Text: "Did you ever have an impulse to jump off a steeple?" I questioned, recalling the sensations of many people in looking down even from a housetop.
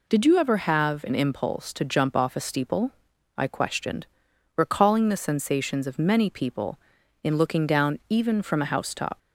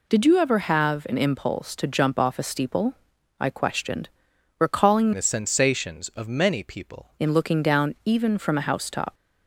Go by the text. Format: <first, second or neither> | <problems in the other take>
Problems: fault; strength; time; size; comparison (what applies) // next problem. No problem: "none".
first | changes voice from "the" to "people"; from 5.1 to 7.0 s; 1.9 s long